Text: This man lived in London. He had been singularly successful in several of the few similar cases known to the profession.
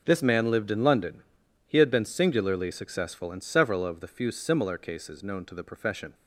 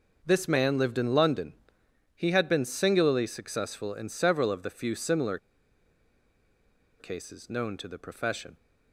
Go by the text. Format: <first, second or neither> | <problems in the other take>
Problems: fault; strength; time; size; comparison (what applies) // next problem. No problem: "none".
first | pauses between "similar" and "cases"; strong; at 5.3 s; 1.6 s long